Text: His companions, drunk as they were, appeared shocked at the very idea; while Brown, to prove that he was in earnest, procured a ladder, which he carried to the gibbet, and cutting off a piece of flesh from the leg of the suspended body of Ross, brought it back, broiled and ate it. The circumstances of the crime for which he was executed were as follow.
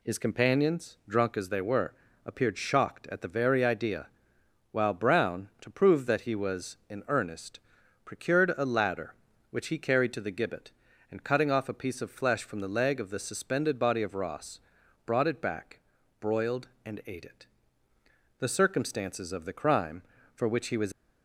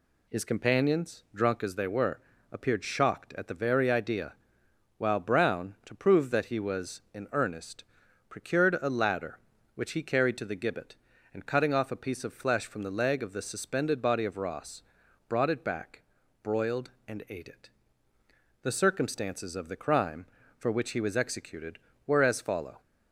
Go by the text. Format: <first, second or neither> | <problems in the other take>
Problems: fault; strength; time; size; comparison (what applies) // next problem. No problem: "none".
second | stops before "executed were as follow"; at 20.9 s